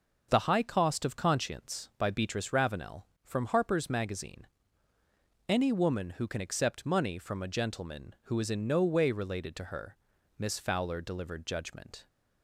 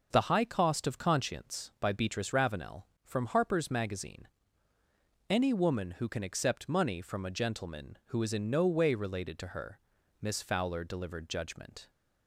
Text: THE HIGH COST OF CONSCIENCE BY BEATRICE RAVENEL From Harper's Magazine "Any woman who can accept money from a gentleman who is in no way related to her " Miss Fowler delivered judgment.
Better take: neither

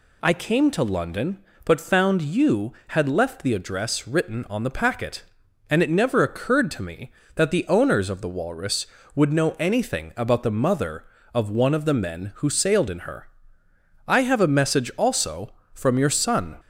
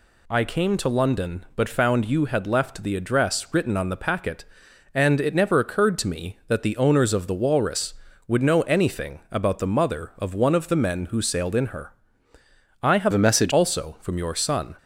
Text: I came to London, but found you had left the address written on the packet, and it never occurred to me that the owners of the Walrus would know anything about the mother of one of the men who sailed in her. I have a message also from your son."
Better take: first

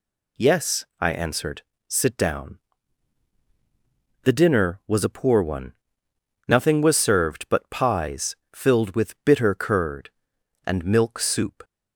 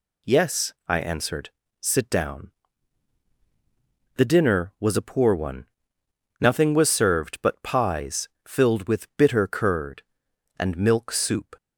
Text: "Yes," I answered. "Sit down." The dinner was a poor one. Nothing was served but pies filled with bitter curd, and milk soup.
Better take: neither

